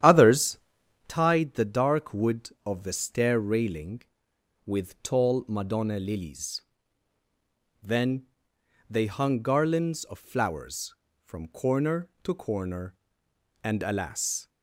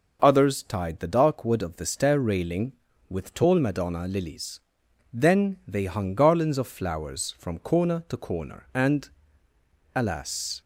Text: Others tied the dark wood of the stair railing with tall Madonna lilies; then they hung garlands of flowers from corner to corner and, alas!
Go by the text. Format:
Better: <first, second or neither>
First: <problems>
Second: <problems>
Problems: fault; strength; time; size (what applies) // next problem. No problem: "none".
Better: second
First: starts louder than the rest; strong; until 1.2 s; 10.5 dB // pauses between "Others" and "tied"; noticeable; at 0.5 s; 0.50 s long // pauses between "then" and "they"; noticeable; at 8.2 s; 0.64 s long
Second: none